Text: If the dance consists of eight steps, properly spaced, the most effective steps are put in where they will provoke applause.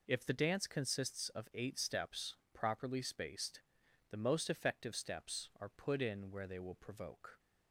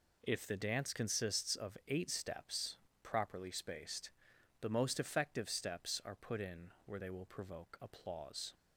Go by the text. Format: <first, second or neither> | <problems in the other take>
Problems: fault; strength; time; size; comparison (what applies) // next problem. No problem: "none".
second | stops before "applause"; at 7.3 s